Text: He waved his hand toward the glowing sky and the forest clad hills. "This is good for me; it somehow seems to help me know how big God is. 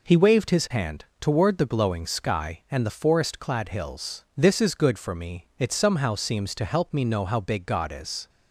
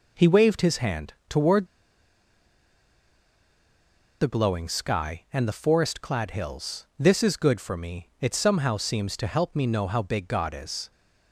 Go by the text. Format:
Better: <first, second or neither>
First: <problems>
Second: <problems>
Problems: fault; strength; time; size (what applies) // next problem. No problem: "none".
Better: first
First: pauses between "hand" and "toward"; slight; at 1.0 s; 0.16 s long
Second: pauses between "hand" and "toward"; slight; at 1.1 s; 0.16 s long // pauses between "toward" and "the"; strong; at 1.6 s; 2.5 s long